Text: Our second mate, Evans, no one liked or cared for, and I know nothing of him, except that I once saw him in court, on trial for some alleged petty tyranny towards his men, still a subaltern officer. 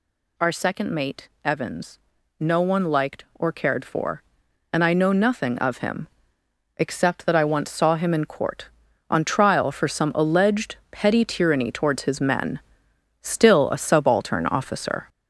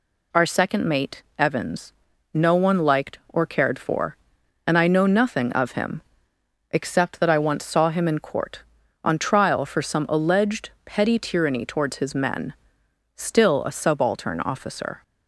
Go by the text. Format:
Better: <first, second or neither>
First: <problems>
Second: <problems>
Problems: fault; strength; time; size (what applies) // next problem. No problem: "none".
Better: second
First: gets louder; noticeable; throughout; 6 dB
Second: none